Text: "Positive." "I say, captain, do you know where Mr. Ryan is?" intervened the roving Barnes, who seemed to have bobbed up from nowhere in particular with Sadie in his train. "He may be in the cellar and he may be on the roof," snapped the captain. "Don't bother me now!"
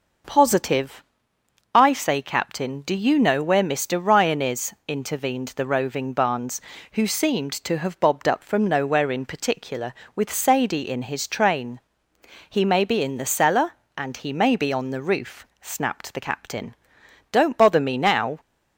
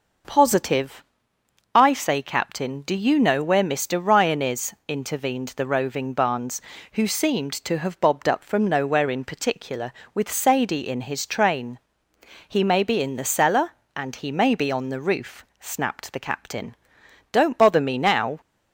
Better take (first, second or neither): neither